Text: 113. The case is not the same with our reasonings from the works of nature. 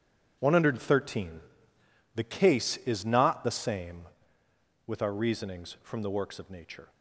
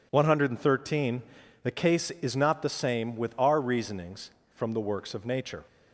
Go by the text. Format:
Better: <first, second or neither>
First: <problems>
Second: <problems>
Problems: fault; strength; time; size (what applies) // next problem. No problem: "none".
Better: second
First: gets quieter; strong; throughout; 11.5 dB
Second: none